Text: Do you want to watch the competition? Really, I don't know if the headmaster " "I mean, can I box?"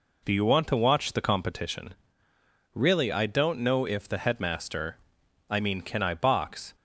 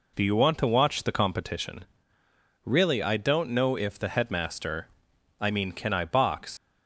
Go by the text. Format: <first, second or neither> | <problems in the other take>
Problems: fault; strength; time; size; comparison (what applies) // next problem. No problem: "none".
first | leaves "box" unfinished; at 6.5 s; 85 ms